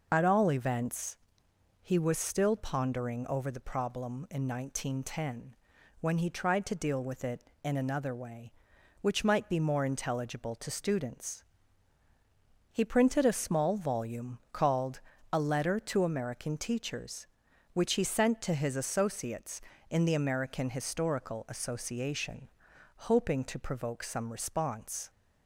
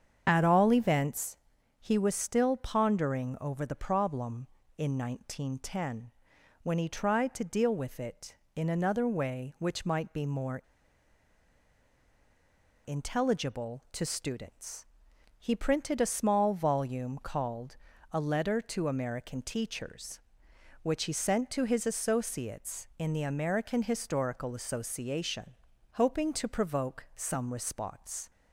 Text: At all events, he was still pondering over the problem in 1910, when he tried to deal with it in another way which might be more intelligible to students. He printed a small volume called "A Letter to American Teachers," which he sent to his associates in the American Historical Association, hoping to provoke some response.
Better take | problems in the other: first | starts louder than the rest; strong; until 1.2 s; 7.5 dB // pauses between "more" and "intelligible"; strong; at 10.5 s; 2.2 s long // pauses between "called" and "A"; slight; at 17.7 s; 0.36 s long; slight in the first

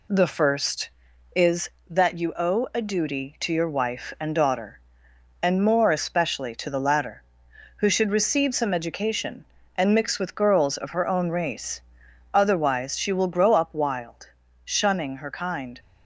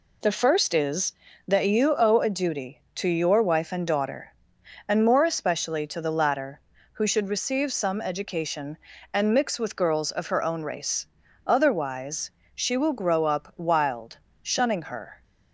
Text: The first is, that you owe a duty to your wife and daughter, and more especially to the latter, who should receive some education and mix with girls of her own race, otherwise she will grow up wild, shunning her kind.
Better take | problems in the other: first | pauses between "otherwise" and "she"; slight; at 12.2 s; 0.24 s long // stops before "kind"; at 15.2 s

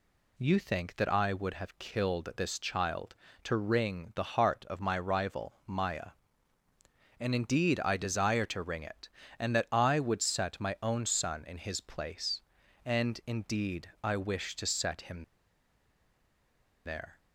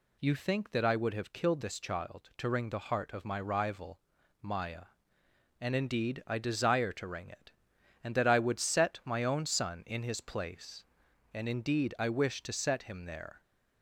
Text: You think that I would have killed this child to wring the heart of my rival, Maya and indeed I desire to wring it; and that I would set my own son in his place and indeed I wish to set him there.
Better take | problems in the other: second | pauses between "him" and "there"; strong; at 15.2 s; 1.6 s long

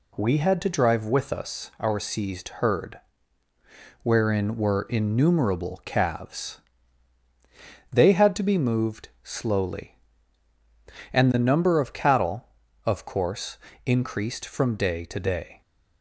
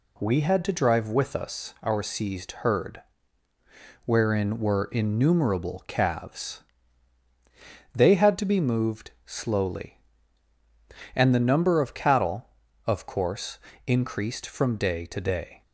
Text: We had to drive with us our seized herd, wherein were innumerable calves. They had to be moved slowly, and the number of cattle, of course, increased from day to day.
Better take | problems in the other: neither | pauses between "moved" and "slowly"; slight; the same in both

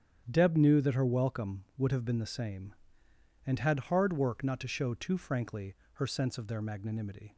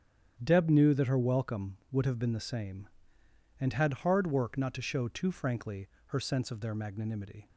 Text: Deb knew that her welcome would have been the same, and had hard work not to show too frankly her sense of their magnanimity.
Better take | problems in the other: neither | starts louder than the rest; strong; the same in both // pauses between "frankly" and "her"; slight; the same in both

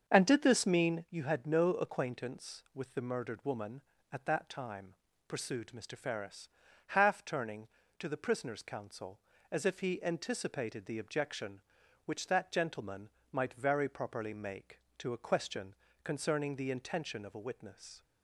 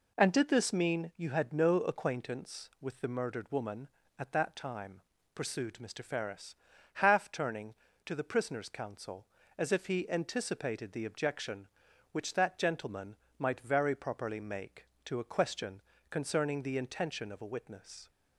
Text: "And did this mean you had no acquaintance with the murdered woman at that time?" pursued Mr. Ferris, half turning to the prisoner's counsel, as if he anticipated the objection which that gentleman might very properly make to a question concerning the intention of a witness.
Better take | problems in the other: second | starts louder than the rest; until 1.1 s; 7 dB // pauses between "gentleman" and "might"; slight; at 13.0 s; 0.24 s long; slight in the second // pauses between "question" and "concerning"; slight; at 15.7 s; 0.30 s long; slight in the second

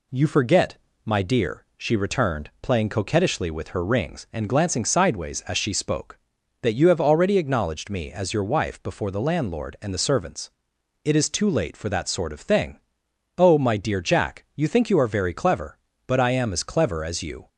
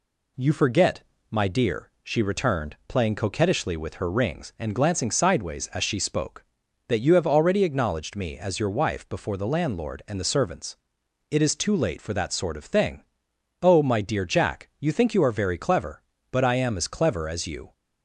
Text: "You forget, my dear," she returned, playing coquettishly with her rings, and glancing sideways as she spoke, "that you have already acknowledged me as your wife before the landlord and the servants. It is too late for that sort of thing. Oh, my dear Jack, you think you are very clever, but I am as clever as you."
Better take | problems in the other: neither | none

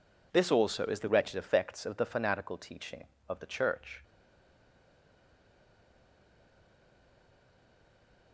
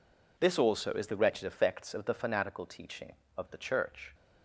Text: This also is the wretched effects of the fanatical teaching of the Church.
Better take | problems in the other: second | stays silent after the last word; strong; from 4.0 s on; 4.3 s long

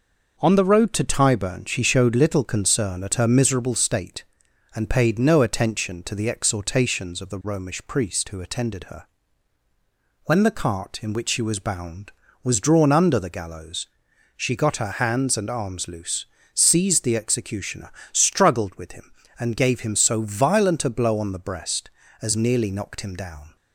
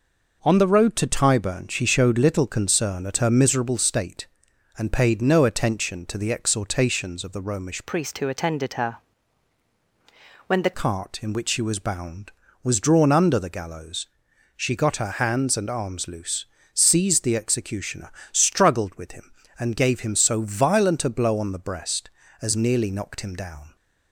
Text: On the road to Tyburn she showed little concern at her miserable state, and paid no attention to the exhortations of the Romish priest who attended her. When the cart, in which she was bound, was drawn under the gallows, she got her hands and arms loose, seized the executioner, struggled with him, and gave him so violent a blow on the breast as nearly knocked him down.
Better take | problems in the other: first | changes voice from "priest" to "the"; from 7.8 to 10.7 s; 2.9 s long

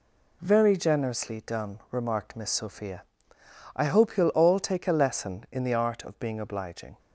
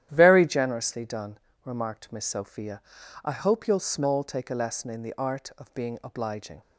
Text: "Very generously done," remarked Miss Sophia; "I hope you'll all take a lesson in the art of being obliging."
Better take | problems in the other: first | starts louder than the rest; strong; until 1.1 s; 11.5 dB // says "small" for "all"; at 3.7 s

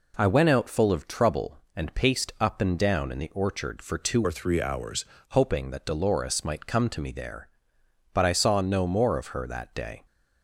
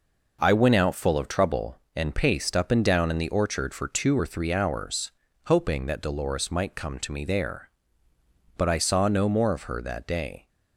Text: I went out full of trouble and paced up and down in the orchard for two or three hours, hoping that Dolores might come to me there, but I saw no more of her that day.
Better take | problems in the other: second | changes voice from "or" to "hours"; from 4.2 to 5.0 s; 0.8 s long

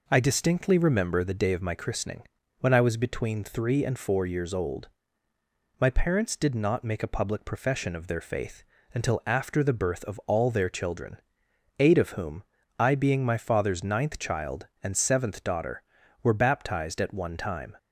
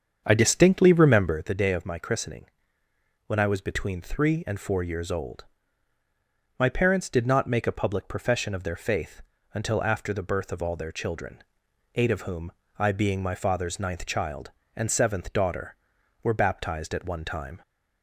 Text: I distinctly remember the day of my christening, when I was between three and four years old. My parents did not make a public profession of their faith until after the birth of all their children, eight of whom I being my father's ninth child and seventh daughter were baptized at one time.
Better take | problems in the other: first | starts louder than the rest; strong; until 1.5 s; 7 dB // pauses between "faith" and "until"; slight; at 9.2 s; 0.32 s long; slight in the first // pauses between "whom" and "I"; slight; at 12.5 s; 0.28 s long; slight in the first

